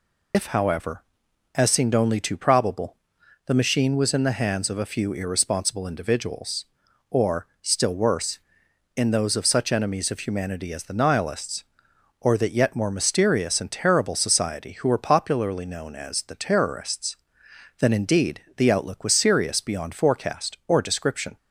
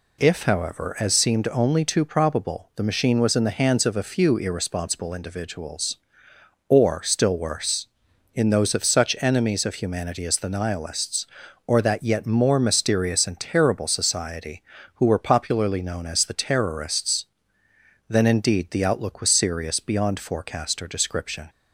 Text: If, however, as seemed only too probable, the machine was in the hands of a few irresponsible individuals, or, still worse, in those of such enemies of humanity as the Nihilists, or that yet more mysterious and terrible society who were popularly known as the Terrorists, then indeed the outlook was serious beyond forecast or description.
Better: second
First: loses the start of "If"; at 0.3 s; 65 ms // pauses between "indeed" and "the"; slight; at 18.4 s; 0.16 s long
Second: none

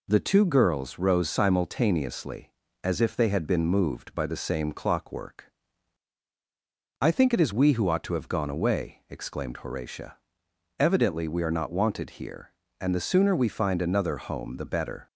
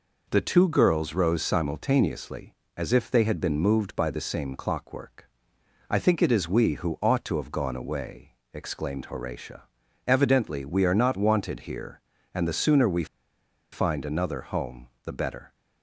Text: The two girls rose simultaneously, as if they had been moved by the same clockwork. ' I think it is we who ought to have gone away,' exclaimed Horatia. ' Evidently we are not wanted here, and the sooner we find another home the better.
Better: first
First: none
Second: pauses between "we" and "find"; noticeable; at 13.0 s; 0.67 s long // pauses between "home" and "the"; slight; at 14.8 s; 0.18 s long

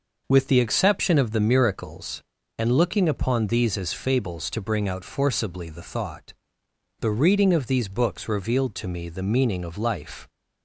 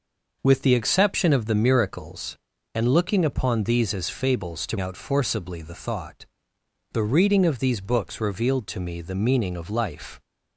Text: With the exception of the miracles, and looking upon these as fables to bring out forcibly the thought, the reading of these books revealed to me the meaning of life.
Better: first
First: none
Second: skips "bring"; at 4.7 s

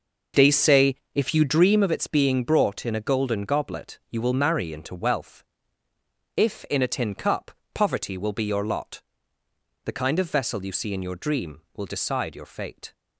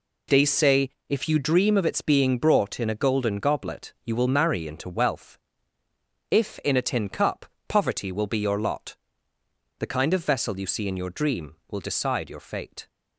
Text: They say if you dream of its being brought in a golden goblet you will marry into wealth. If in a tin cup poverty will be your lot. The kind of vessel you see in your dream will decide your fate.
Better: second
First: starts louder than the rest; noticeable; until 1.9 s; 5.5 dB // pauses between "say" and "if"; slight; at 0.9 s; 0.16 s long // pauses between "cup" and "poverty"; slight; at 7.5 s; 0.22 s long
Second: pauses between "say" and "if"; slight; at 0.9 s; 0.16 s long // pauses between "cup" and "poverty"; slight; at 7.4 s; 0.22 s long

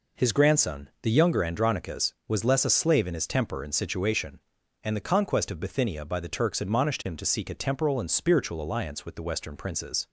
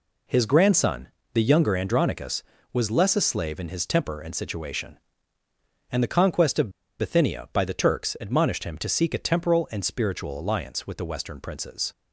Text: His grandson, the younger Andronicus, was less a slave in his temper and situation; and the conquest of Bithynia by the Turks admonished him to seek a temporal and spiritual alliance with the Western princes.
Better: first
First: none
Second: pauses between "of" and "Bithynia"; slight; at 6.6 s; 0.29 s long

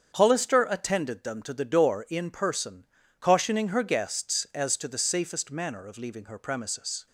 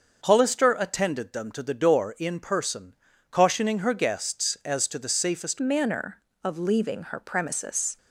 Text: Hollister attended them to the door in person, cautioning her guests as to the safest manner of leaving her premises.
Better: first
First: starts louder than the rest; strong; until 1.1 s; 7.5 dB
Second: starts louder than the rest; until 1.2 s; 6.5 dB // changes voice at "manner"; from 5.5 s on; 2.4 s long

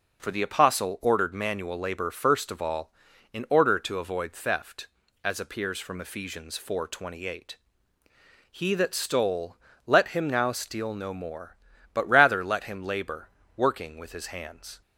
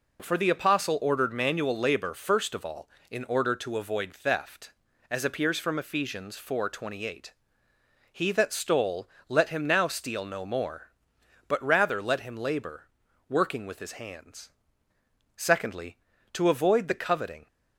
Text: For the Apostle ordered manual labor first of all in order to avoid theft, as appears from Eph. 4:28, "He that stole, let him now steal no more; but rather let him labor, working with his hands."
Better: first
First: none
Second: goes on to say "Secondly to avoid the coveting"; strong; from 15.3 s on; 2.1 s long

